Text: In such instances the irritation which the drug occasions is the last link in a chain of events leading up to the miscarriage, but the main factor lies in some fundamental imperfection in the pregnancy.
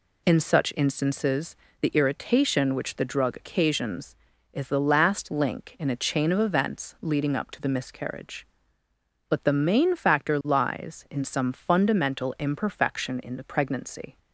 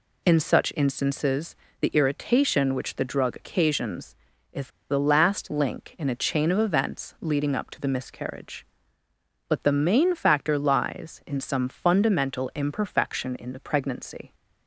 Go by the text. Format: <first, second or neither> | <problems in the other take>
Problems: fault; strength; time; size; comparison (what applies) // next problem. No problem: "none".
first | pauses between "instances" and "the"; slight; at 1.5 s; 0.26 s long; slight in the first // pauses between "is" and "the"; slight; at 4.6 s; 0.22 s long